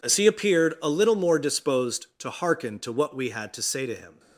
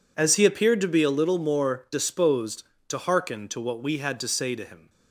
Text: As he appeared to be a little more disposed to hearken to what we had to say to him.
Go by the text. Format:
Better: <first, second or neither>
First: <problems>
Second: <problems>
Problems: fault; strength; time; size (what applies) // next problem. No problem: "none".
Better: second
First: skips "to be"; at 0.7 s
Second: none